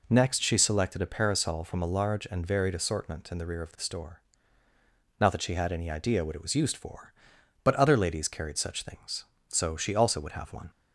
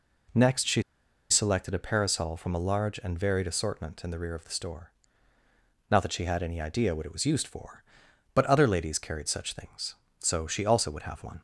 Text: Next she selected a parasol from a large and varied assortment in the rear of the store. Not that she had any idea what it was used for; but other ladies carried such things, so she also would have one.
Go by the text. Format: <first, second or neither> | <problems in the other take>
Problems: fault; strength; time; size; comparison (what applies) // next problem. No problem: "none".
first | pauses between "she" and "selected"; noticeable; at 0.8 s; 0.48 s long